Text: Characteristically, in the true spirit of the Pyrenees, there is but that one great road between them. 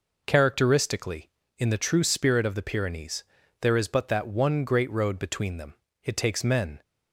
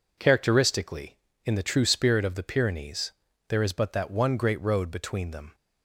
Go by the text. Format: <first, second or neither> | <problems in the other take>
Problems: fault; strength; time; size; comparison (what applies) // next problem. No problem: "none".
second | goes on to say "It takes men"; noticeable; from 6.0 s on; 0.78 s long